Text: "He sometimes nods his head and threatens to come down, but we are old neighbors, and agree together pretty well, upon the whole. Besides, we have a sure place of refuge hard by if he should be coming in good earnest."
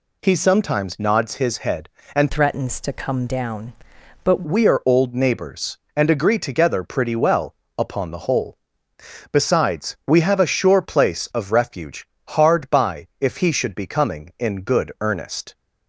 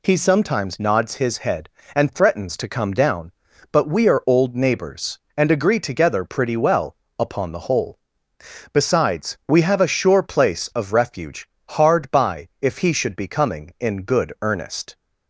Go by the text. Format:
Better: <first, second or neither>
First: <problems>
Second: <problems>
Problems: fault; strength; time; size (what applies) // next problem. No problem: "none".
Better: second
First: changes voice from "threatens" to "but"; from 2.3 to 4.4 s; 2.1 s long // pauses between "refuge" and "hard"; slight; at 12.0 s; 0.22 s long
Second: pauses between "refuge" and "hard"; slight; at 11.4 s; 0.22 s long